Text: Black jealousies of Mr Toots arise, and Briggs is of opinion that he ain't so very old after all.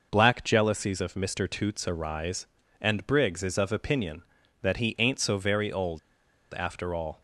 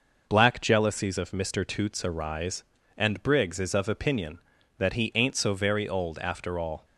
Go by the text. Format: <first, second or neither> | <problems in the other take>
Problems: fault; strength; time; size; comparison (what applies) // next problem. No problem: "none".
second | pauses between "old" and "after"; noticeable; at 5.9 s; 0.54 s long